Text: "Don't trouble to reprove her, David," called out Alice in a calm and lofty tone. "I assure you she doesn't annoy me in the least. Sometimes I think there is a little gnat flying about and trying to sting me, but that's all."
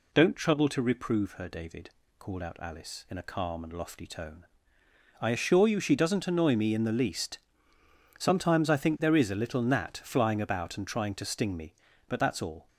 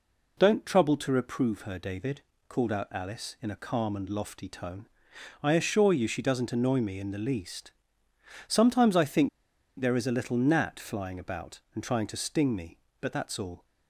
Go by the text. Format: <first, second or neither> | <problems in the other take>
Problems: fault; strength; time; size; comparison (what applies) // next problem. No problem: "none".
first | pauses between "think" and "there"; noticeable; at 9.2 s; 0.50 s long